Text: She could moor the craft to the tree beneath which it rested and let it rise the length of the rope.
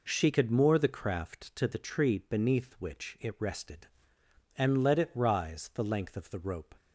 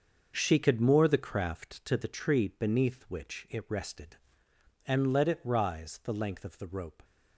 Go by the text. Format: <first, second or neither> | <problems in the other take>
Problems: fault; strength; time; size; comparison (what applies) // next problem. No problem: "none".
first | gets quieter; strong; throughout; 9 dB